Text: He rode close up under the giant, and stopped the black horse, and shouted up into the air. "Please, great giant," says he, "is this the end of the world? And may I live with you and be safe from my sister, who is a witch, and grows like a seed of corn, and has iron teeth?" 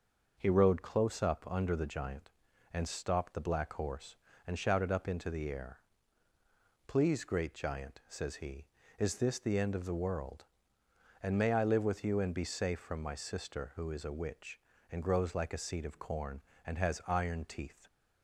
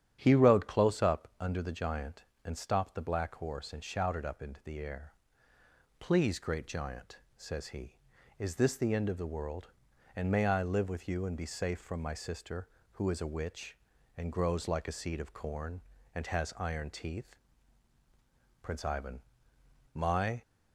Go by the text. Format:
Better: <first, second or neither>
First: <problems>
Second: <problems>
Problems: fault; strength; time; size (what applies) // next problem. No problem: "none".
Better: first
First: none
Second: starts louder than the rest; strong; until 1.2 s; 10 dB // goes on to say "Prince Ivan my"; strong; from 18.6 s on; 1.8 s long